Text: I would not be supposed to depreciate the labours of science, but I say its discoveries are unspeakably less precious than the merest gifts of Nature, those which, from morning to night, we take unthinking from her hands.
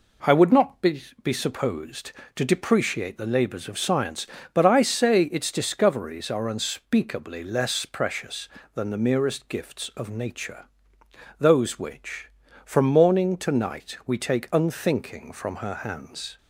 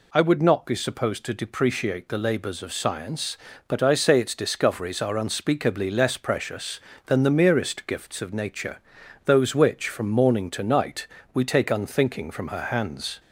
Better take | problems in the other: second | says "be" twice; at 1.2 s

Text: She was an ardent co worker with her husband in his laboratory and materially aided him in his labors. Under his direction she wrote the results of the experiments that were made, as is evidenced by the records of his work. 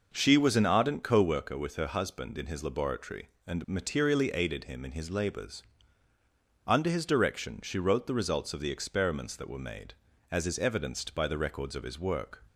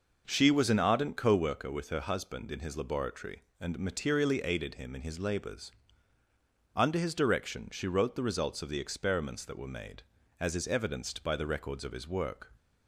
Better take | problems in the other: neither | none

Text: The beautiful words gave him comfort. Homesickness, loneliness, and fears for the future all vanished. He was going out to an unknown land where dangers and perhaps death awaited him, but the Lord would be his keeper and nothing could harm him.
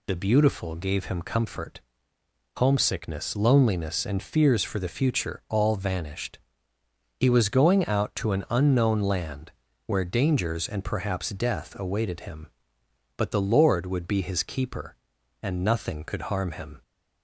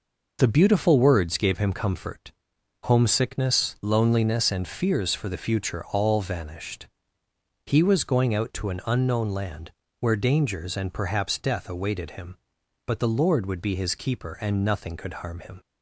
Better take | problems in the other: second | skips "words"; at 0.7 s // pauses between "land" and "where"; slight; at 9.5 s; 0.36 s long; slight in the second

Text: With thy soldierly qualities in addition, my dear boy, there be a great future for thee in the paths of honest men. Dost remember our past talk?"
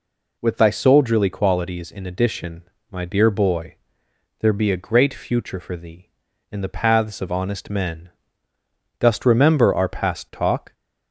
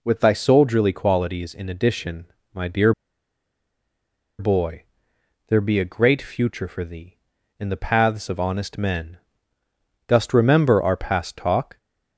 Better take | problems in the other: first | pauses between "dear" and "boy"; strong; at 2.9 s; 1.4 s long

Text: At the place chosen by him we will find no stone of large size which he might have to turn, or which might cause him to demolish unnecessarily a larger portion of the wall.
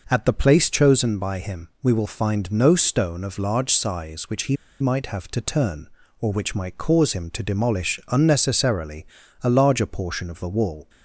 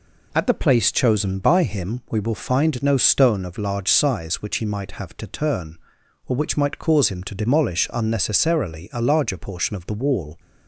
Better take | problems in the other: second | pauses between "he" and "might"; slight; at 4.5 s; 0.25 s long // pauses between "unnecessarily" and "a"; slight; at 9.0 s; 0.34 s long

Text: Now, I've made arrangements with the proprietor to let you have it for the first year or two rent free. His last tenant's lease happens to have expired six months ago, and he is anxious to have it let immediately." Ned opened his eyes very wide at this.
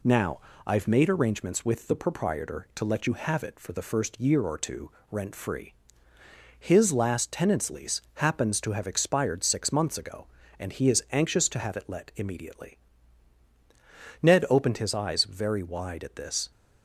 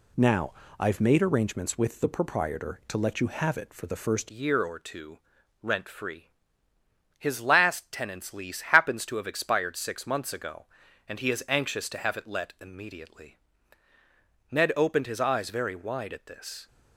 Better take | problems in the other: first | changes voice at "year"; from 4.3 s on; 12.3 s long // pauses between "two" and "rent"; at 5.1 s; 0.44 s long; slight in the first

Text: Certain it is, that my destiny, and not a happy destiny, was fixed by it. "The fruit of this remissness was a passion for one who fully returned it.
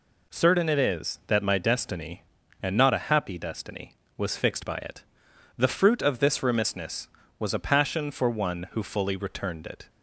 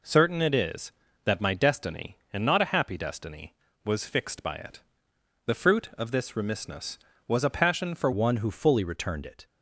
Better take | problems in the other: first | changes voice at "one"; from 8.1 s on; 1.3 s long

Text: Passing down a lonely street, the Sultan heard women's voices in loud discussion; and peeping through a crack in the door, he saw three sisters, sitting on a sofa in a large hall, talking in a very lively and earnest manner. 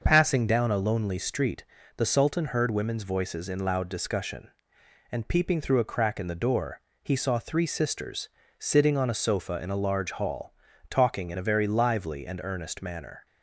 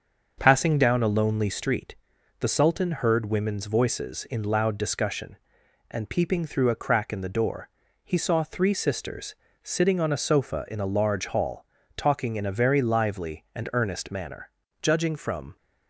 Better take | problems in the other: first | starts louder than the rest; until 1.3 s; 6.5 dB; also in the first // goes on to say "Judging from"; noticeable; from 14.8 s on; 0.76 s long

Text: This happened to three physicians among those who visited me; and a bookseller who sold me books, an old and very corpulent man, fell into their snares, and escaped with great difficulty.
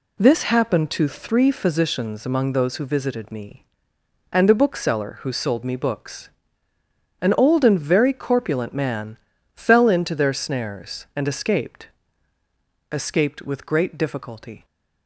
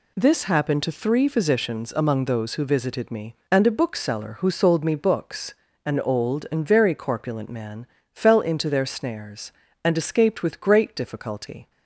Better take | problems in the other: second | says "escaped" twice; at 12.9 s

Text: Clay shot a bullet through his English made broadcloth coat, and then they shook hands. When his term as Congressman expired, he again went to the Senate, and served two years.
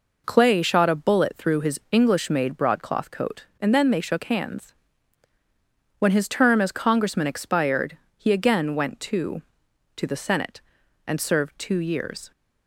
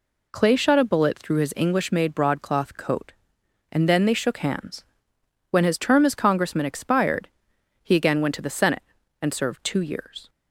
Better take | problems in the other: second | says "to" twice; at 9.9 s

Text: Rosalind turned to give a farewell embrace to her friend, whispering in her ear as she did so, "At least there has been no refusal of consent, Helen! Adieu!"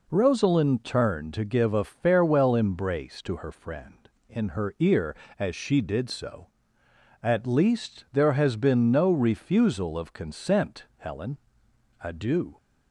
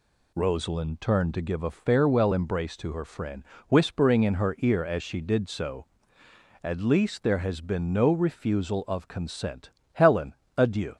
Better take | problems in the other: second | skips "whispering"; at 4.2 s

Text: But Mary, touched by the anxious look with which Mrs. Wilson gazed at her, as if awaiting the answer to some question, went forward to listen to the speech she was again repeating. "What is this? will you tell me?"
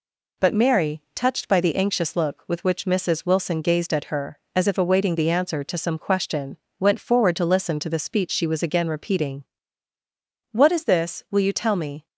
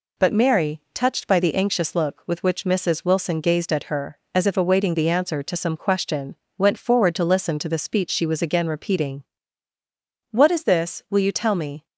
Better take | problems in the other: neither | none

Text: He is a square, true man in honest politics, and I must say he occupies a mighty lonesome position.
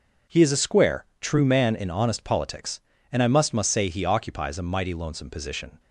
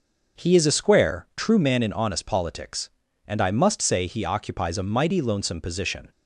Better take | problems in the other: second | starts louder than the rest; until 1.4 s; 6.5 dB // says "must" twice; at 3.5 s

